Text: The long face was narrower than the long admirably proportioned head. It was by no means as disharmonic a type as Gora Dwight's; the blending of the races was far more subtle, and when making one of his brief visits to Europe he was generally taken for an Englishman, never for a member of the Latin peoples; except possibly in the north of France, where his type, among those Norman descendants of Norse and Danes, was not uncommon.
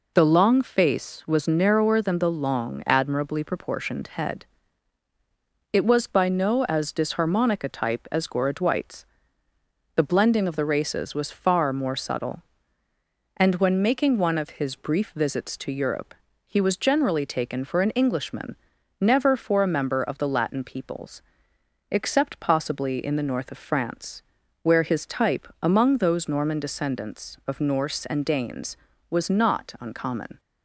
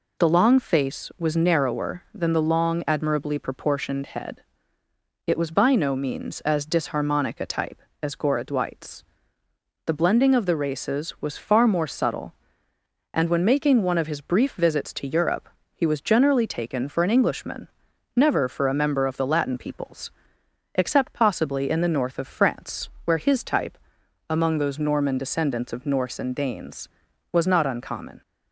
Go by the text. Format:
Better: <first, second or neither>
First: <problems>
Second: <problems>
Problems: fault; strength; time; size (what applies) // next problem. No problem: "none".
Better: second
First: skips "means"; at 6.6 s // pauses between "Europe" and "he"; slight; at 16.1 s; 0.32 s long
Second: pauses between "Europe" and "he"; slight; at 15.4 s; 0.28 s long